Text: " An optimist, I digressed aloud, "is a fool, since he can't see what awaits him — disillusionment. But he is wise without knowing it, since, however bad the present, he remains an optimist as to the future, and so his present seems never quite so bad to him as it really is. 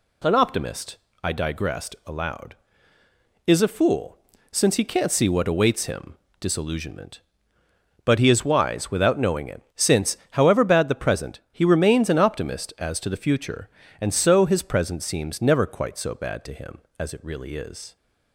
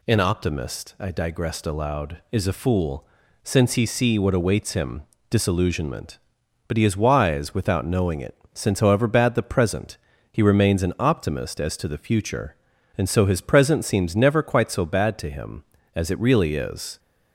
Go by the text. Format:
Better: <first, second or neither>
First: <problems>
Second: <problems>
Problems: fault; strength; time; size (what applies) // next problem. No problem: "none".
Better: first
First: none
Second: skips "can't"; at 3.8 s